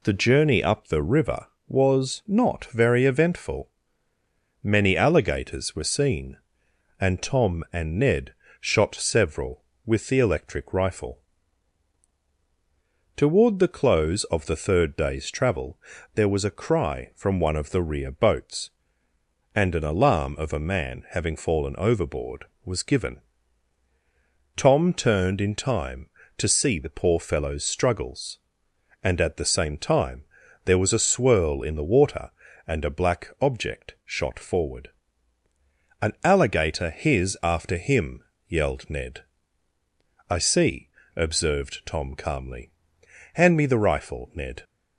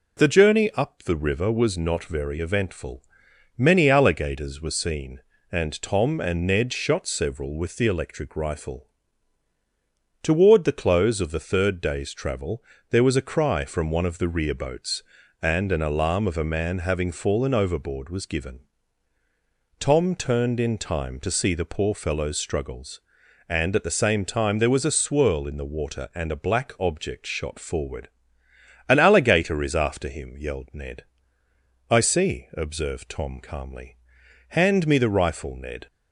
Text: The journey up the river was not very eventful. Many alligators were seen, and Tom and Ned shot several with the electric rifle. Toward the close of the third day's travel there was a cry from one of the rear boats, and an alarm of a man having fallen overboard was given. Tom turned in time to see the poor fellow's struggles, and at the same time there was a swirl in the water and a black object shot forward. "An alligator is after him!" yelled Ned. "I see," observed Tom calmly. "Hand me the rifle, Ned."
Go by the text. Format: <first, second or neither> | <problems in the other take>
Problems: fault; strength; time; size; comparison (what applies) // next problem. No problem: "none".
second | pauses between "Ned" and "shot"; slight; at 8.3 s; 0.28 s long // pauses between "travel" and "there"; at 15.7 s; 0.38 s long; slight in the second // pauses between "time" and "there"; at 30.2 s; 0.42 s long // says "his" for "is"; at 36.8 s